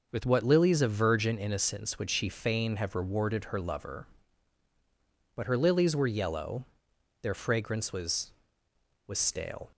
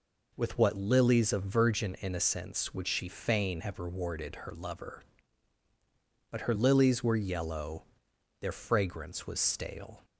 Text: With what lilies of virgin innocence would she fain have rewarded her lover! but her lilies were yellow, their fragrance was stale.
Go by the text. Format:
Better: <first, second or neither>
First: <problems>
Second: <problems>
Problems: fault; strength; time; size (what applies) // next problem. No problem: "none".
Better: second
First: says "was" twice; at 9.0 s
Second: none